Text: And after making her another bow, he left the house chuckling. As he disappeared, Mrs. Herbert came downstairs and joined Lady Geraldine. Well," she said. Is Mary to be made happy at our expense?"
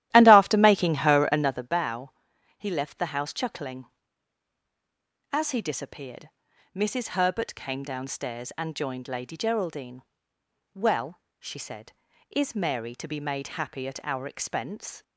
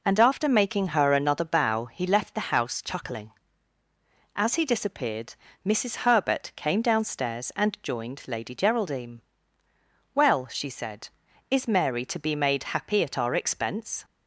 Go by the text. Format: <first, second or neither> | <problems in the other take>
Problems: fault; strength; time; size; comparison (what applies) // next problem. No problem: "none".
second | starts louder than the rest; strong; until 1.7 s; 13.5 dB